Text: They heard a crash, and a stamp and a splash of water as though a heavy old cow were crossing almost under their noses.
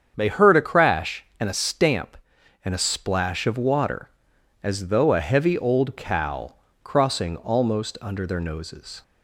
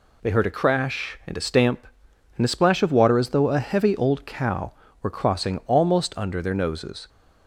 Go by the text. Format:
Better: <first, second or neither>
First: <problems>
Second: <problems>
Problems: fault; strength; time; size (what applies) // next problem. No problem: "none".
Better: second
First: starts louder than the rest; strong; until 1.1 s; 7.5 dB // skips "were"; at 6.6 s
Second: none